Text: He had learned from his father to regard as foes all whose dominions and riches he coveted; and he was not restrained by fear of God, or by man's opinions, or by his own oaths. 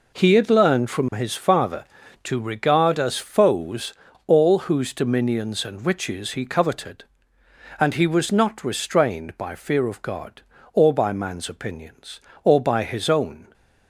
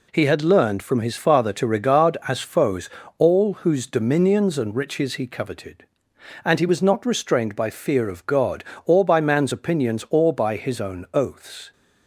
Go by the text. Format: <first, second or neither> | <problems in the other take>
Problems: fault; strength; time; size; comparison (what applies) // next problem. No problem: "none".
second | pauses between "foes" and "all"; slight; at 3.9 s; 0.32 s long; slight in the second // stops before "oaths"; at 13.5 s